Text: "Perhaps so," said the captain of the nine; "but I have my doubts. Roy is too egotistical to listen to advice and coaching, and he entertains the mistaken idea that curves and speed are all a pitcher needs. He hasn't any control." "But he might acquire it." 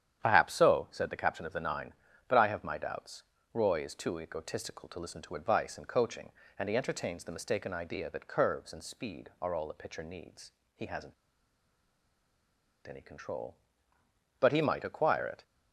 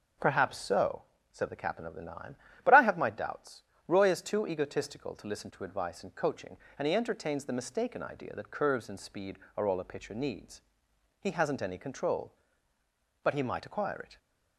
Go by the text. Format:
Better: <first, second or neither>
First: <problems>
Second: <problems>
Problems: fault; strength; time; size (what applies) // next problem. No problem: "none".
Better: second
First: starts louder than the rest; strong; until 1.2 s; 9.5 dB // pauses between "hasn't" and "any"; strong; at 11.1 s; 1.7 s long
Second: none